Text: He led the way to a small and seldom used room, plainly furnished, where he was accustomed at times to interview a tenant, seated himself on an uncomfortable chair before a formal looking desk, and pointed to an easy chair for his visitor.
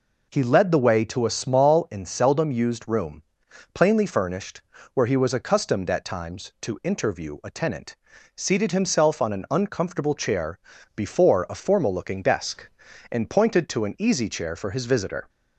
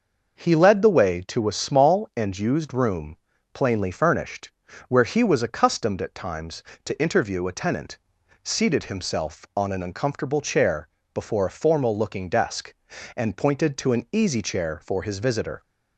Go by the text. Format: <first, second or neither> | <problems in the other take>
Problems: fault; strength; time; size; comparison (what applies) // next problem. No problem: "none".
first | skips "seldom"; at 2.3 s // pauses between "chair" and "before"; slight; at 10.8 s; 0.26 s long; slight in the first